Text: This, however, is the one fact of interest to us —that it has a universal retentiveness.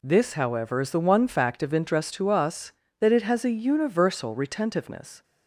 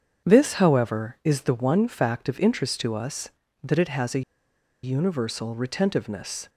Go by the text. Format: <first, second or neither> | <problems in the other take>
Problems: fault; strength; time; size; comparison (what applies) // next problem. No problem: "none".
first | starts louder than the rest; strong; until 1.3 s; 7.5 dB // pauses between "a" and "universal"; noticeable; at 4.2 s; 0.62 s long